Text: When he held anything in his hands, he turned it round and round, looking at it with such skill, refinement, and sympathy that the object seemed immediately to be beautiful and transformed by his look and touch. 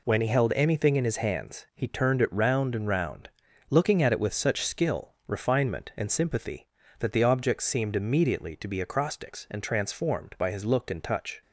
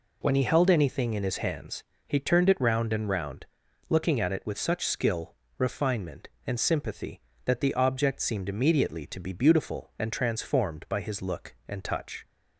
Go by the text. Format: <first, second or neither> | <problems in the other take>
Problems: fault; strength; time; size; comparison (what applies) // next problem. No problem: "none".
second | says "acrostics" for "beautiful"; at 8.8 s